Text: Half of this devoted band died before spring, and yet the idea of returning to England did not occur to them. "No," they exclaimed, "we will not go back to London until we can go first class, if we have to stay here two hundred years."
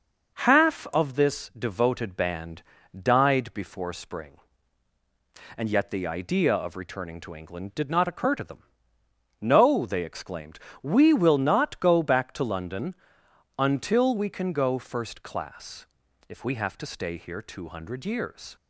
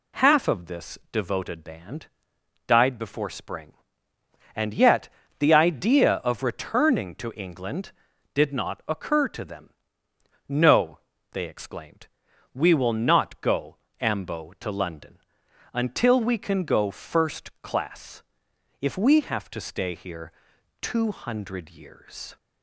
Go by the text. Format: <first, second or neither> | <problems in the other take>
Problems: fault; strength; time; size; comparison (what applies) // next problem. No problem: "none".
first | pauses between "band" and "died"; noticeable; at 2.0 s; 0.62 s long; slight in the first // pauses between "yet" and "the"; slight; at 5.0 s; 0.32 s long // says "ambo" for "back"; at 13.9 s // pauses between "London" and "until"; noticeable; at 15.1 s; 0.54 s long; noticeable in the first // pauses between "here" and "two"; noticeable; at 20.3 s; 0.50 s long